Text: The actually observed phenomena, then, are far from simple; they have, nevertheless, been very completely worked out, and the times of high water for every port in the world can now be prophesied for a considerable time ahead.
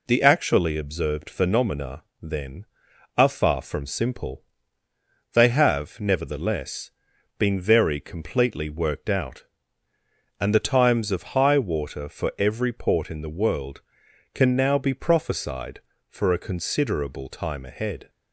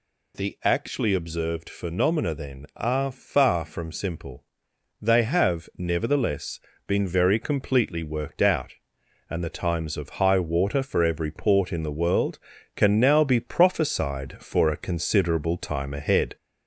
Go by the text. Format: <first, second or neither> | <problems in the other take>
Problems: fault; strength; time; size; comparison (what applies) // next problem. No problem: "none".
first | gets louder; slight; throughout; 3 dB